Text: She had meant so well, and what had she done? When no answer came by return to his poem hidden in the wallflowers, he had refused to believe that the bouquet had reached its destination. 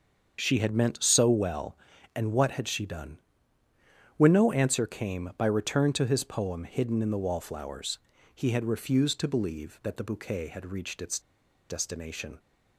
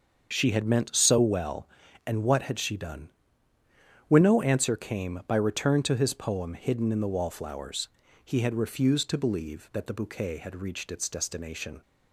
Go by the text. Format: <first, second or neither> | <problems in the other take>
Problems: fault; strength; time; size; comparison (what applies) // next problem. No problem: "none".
second | starts louder than the rest; until 1.4 s; 7 dB; also in the second // pauses between "its" and "destination"; noticeable; at 11.1 s; 0.50 s long